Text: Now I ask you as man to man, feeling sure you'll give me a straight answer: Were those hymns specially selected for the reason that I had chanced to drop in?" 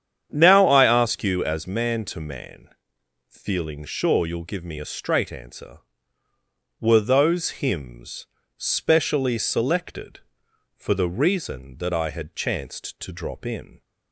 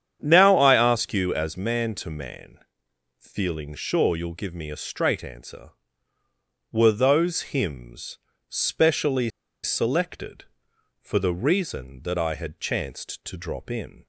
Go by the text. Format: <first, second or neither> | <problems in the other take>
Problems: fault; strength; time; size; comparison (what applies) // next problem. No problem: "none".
first | starts louder than the rest; strong; until 1.2 s; 8.5 dB; strong in the first // pauses between "hymns" and "specially"; slight; at 8.1 s; 0.28 s long; slight in the first // pauses between "specially" and "selected"; slight; at 9.3 s; 0.33 s long